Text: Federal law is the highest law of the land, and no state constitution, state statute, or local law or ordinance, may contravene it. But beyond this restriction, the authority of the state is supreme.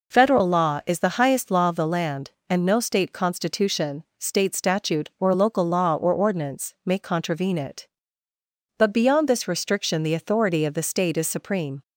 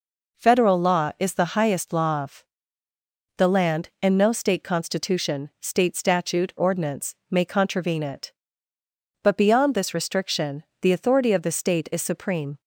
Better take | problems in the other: first | pauses between "of" and "the"; noticeable; at 2.4 s; 0.92 s long // skips "or local law or"; at 6.5 s

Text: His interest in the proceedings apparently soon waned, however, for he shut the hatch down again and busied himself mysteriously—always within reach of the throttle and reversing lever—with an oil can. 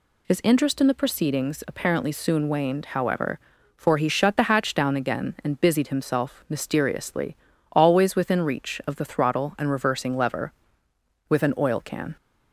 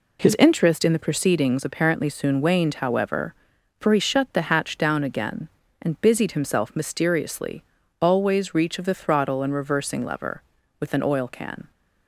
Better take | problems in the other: first | skips "within"; at 8.5 s

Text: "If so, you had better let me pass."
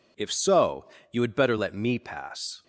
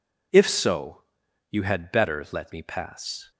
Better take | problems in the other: neither | none

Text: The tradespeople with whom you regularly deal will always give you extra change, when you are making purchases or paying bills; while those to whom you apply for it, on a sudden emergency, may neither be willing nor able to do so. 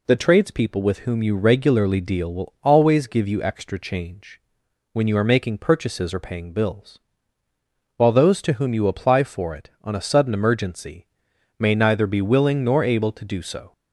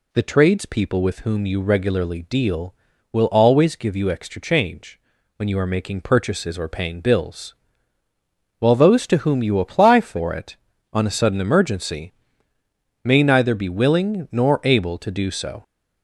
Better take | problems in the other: neither | none

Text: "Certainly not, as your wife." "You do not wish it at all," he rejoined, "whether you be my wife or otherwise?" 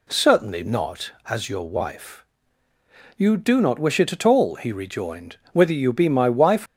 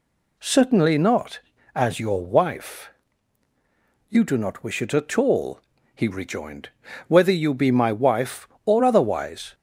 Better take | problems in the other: second | stops before "or otherwise"; at 6.6 s

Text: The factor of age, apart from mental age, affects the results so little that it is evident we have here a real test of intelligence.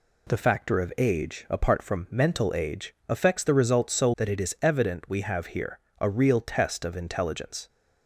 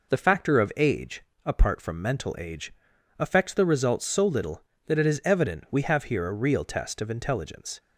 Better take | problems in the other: second | skips "little"; at 4.1 s // pauses between "here" and "a"; slight; at 5.7 s; 0.20 s long

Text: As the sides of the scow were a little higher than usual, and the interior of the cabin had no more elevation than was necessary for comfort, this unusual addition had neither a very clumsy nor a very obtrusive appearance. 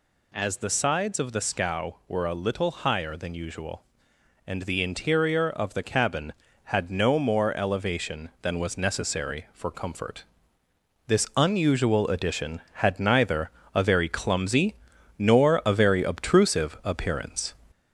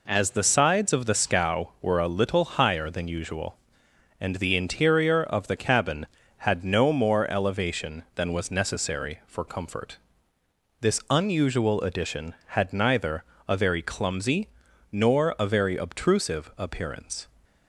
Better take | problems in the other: second | gets louder; slight; throughout; 3 dB // pauses between "neither" and "a"; slight; at 13.5 s; 0.24 s long; slight in the second // pauses between "clumsy" and "nor"; noticeable; at 14.7 s; 0.46 s long; noticeable in the second

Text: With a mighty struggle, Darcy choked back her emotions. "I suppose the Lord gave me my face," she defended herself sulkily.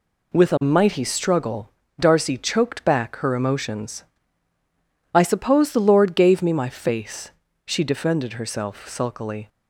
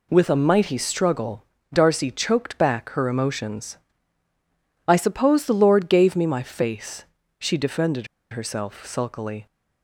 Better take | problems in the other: first | pauses between "defended" and "herself"; slight; at 8.0 s; 0.24 s long

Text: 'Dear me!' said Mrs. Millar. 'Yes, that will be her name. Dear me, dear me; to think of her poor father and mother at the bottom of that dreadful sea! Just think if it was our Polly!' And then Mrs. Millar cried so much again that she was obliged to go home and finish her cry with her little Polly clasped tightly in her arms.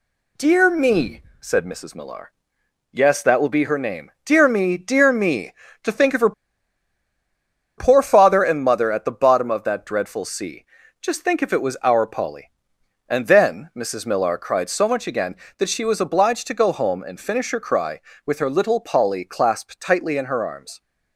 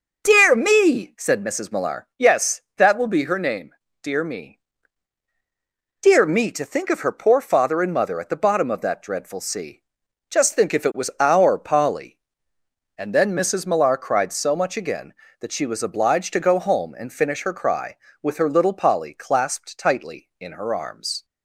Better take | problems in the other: second | pauses between "her" and "poor"; strong; at 6.3 s; 1.4 s long

